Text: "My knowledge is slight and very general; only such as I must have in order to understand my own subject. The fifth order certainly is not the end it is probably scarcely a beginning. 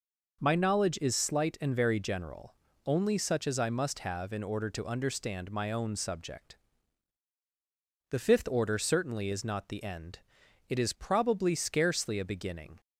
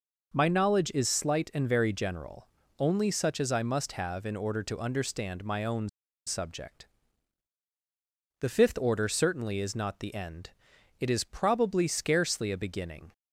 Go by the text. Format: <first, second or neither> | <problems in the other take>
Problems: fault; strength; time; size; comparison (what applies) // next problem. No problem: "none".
first | pauses between "own" and "subject"; at 5.8 s; 0.37 s long // pauses between "end" and "it"; noticeable; at 10.5 s; 0.50 s long; noticeable in the first